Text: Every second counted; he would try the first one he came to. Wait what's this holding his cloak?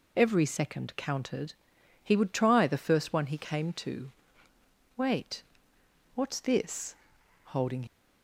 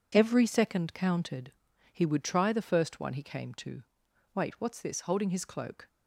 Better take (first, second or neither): second